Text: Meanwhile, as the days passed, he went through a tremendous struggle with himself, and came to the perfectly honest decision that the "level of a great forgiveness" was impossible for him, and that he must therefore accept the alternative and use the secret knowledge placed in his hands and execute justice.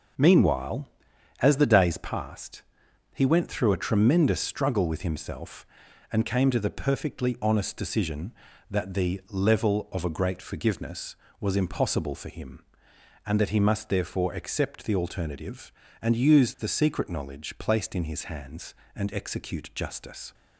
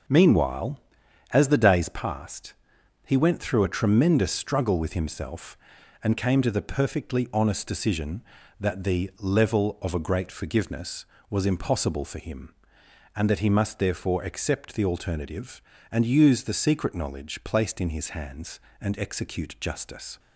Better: neither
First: none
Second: none

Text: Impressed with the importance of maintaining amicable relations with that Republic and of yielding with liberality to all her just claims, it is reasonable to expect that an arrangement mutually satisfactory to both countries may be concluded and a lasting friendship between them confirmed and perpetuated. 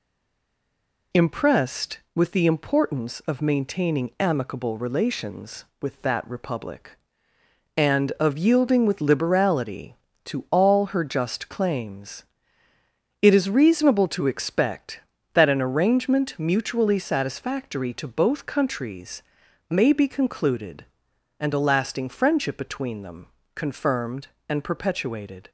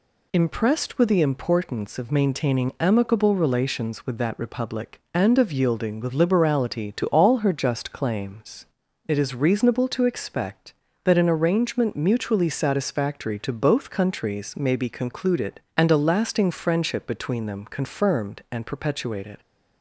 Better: second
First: stays silent before the first word; until 1.1 s; 1.1 s long // pauses between "countries" and "may"; noticeable; at 19.2 s; 0.48 s long // pauses between "them" and "confirmed"; slight; at 23.2 s; 0.28 s long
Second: none

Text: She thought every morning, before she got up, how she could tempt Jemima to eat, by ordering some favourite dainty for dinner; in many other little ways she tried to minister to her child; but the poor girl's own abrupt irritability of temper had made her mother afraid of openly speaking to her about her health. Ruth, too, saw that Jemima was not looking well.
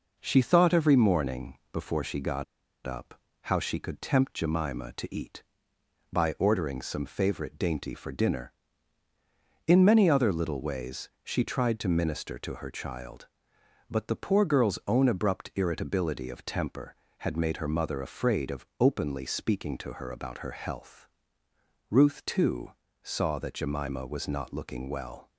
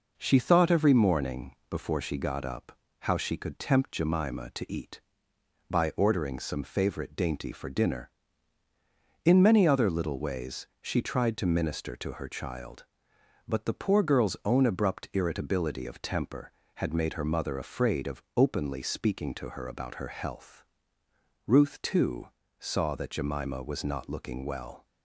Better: second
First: pauses between "got" and "up"; at 2.4 s; 0.42 s long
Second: none

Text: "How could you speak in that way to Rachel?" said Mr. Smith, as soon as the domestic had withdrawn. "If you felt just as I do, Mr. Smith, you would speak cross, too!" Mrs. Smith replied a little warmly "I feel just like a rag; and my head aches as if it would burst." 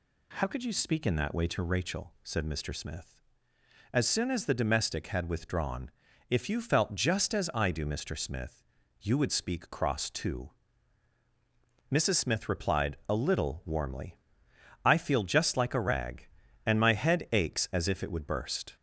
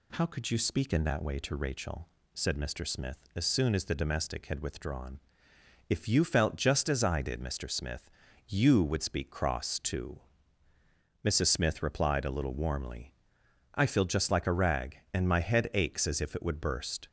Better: first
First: pauses between "warmly" and "I"; noticeable; at 14.1 s; 0.66 s long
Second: says "did" for "do"; at 7.2 s // pauses between "warmly" and "I"; noticeable; at 13.1 s; 0.60 s long

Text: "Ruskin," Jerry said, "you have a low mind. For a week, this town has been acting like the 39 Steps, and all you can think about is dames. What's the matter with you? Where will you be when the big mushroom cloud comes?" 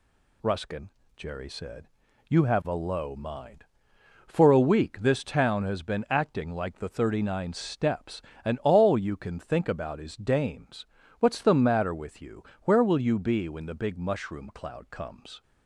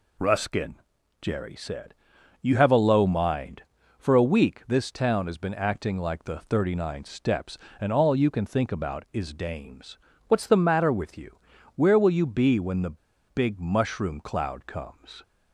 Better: first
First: none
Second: pauses between "the" and "big"; slight; at 12.9 s; 0.31 s long

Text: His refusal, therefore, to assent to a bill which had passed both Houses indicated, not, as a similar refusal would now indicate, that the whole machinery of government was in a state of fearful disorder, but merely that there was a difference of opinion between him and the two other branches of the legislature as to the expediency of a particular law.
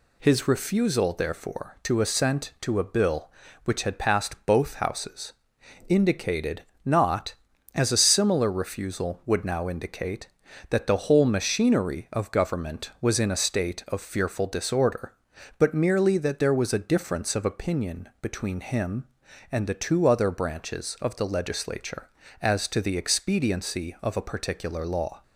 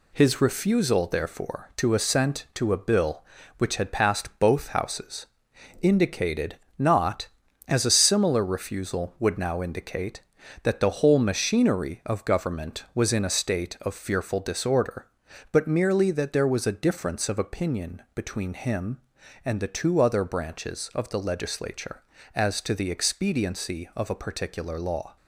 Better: first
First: pauses between "Houses" and "indicated"; noticeable; at 5.3 s; 0.56 s long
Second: gets quieter; noticeable; throughout; 5 dB // pauses between "Houses" and "indicated"; noticeable; at 5.2 s; 0.56 s long

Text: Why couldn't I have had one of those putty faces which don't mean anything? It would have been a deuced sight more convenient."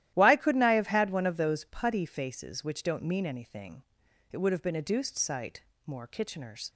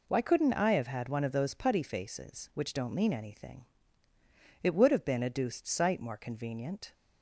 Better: second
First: starts louder than the rest; strong; until 1.1 s; 13.5 dB // pauses between "sight" and "more"; slight; at 5.6 s; 0.24 s long // says "kitcheners" for "convenient"; at 6.0 s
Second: none

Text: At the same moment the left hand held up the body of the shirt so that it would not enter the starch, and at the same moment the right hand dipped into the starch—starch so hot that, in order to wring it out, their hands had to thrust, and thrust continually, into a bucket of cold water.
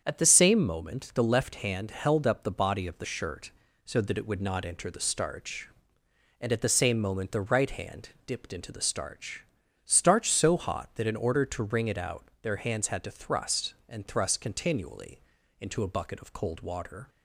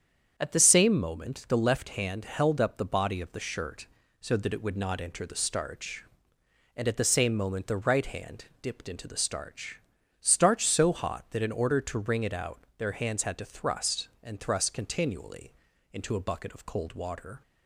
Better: neither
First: starts louder than the rest; strong; until 1.0 s; 7.5 dB // pauses between "hand" and "dipped"; slight; at 8.0 s; 0.16 s long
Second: starts louder than the rest; strong; until 1.3 s; 7.5 dB // pauses between "hand" and "dipped"; slight; at 8.4 s; 0.16 s long

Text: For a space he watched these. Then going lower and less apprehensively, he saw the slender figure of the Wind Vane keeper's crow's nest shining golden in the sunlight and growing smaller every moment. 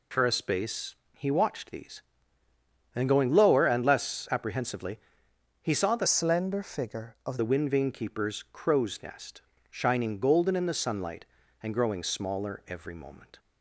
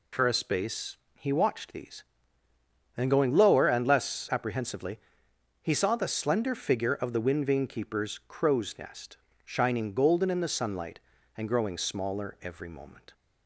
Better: second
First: pauses between "space" and "he"; slight; at 0.9 s; 0.22 s long // changes voice from "slender" to "of"; from 6.0 to 7.3 s; 1.3 s long // pauses between "nest" and "shining"; slight; at 9.4 s; 0.30 s long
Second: pauses between "space" and "he"; slight; at 0.9 s; 0.22 s long // pauses between "nest" and "shining"; slight; at 9.1 s; 0.28 s long

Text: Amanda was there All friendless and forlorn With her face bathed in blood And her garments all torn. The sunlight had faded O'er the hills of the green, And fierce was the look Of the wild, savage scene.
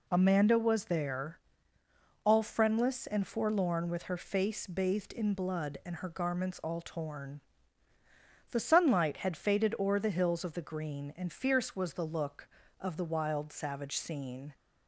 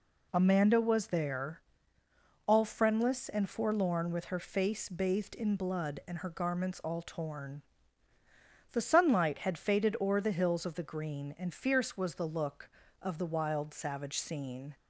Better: neither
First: pauses between "there" and "All"; noticeable; at 1.3 s; 0.88 s long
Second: pauses between "there" and "All"; noticeable; at 1.5 s; 0.88 s long

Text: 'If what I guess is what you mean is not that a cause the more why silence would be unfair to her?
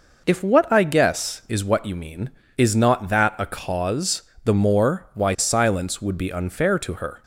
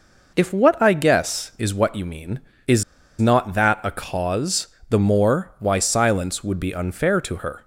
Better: first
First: pauses between "cause" and "the"; slight; at 4.2 s; 0.24 s long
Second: pauses between "is" and "not"; slight; at 2.8 s; 0.35 s long // pauses between "cause" and "the"; slight; at 4.6 s; 0.24 s long

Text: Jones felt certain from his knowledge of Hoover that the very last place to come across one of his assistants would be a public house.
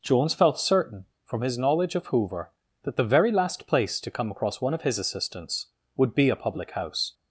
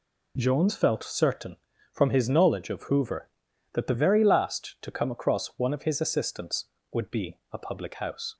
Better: first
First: none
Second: skips "place"; at 4.7 s // pauses between "be" and "a"; slight; at 7.3 s; 0.16 s long

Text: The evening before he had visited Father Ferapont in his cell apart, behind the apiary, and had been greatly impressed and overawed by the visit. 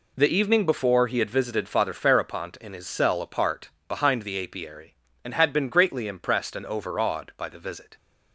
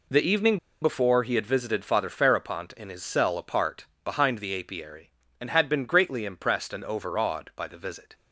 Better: first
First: none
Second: pauses between "evening" and "before"; slight; at 0.5 s; 0.24 s long

